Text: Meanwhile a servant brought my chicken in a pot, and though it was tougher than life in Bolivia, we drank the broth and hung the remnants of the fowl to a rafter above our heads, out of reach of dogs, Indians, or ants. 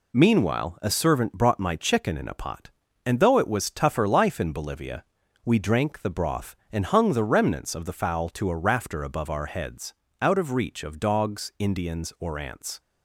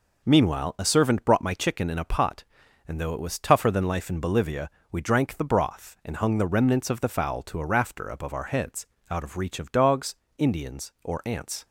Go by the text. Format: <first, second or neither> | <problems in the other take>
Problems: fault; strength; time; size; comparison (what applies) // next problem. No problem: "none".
second | skips "than"; at 4.0 s